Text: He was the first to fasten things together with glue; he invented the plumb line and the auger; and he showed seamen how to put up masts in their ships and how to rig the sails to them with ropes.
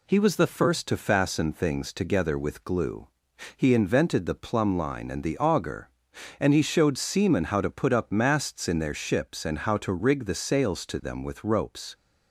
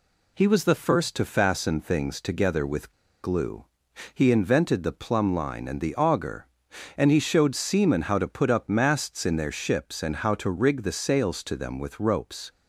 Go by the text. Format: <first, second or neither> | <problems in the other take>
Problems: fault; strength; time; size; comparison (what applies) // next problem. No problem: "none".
first | pauses between "with" and "glue"; slight; at 2.9 s; 0.32 s long